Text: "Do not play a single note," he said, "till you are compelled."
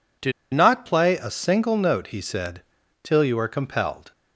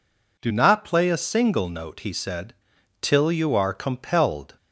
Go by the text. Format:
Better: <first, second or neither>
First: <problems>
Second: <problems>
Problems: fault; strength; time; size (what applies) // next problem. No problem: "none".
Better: second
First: pauses between "Do" and "not"; slight; at 0.3 s; 0.21 s long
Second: none